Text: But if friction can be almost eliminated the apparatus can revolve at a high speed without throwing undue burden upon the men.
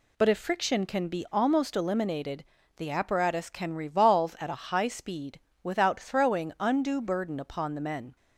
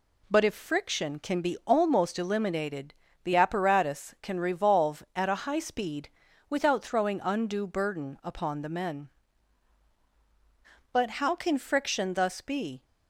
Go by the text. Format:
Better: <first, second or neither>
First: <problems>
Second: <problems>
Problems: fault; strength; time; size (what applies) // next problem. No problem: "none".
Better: first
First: pauses between "eliminated" and "the"; slight; at 2.4 s; 0.34 s long // pauses between "speed" and "without"; slight; at 5.3 s; 0.22 s long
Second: pauses between "eliminated" and "the"; slight; at 2.9 s; 0.28 s long // pauses between "speed" and "without"; at 6.0 s; 0.40 s long // goes on to say "But how can friction thus be"; strong; from 10.9 s on; 1.9 s long